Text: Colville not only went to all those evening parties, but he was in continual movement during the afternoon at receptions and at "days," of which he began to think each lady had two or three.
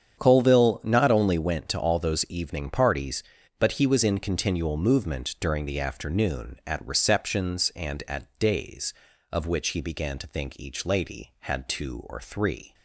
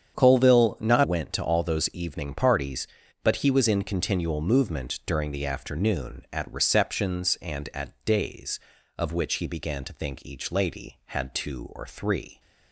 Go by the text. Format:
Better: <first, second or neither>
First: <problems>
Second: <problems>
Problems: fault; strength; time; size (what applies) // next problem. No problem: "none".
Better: first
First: starts louder than the rest; strong; until 1.2 s; 8.5 dB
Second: starts louder than the rest; strong; until 1.1 s; 8 dB // skips "only"; at 1.0 s